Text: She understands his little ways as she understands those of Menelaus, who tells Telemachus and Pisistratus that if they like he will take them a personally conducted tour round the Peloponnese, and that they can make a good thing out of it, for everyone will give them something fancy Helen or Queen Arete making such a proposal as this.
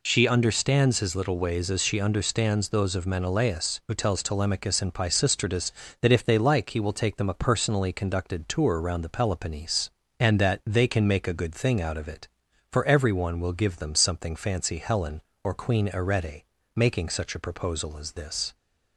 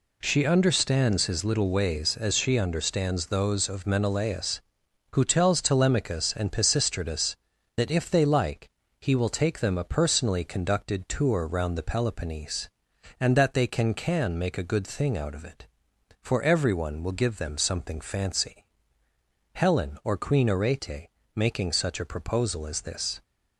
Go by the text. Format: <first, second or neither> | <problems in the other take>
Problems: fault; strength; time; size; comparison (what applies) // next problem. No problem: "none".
first | pauses between "like" and "he"; slight; at 8.6 s; 0.30 s long // says "can" twice; at 13.9 s // pauses between "fancy" and "Helen"; noticeable; at 18.6 s; 0.90 s long // pauses between "Arete" and "making"; slight; at 21.0 s; 0.24 s long; slight in the first